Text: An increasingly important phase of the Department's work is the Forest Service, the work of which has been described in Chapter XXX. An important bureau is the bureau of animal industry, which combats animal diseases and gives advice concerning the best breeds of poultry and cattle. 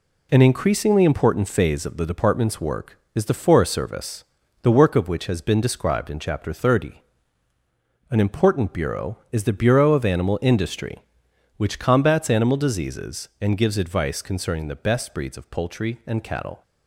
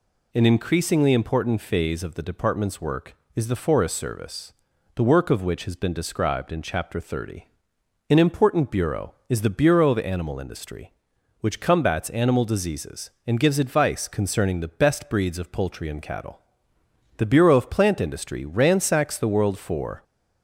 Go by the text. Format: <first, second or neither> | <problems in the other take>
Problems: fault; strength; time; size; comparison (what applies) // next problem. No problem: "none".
first | goes on to say "The bureau of plant industry ransacks the world for"; strong; from 17.1 s on; 2.8 s long